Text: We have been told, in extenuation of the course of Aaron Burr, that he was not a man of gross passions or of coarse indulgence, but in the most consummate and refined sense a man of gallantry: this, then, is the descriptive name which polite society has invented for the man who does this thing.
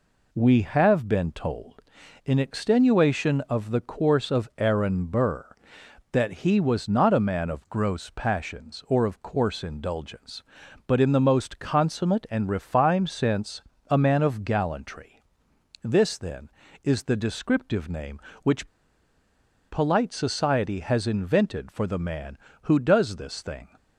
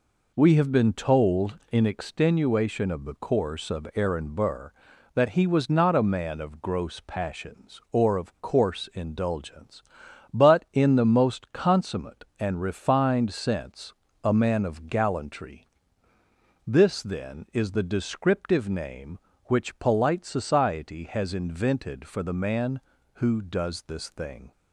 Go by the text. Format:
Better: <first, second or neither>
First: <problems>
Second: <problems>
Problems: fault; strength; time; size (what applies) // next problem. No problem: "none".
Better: second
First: pauses between "sense" and "a"; slight; at 13.6 s; 0.28 s long // pauses between "which" and "polite"; at 18.6 s; 1.0 s long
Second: pauses between "sense" and "a"; slight; at 13.9 s; 0.32 s long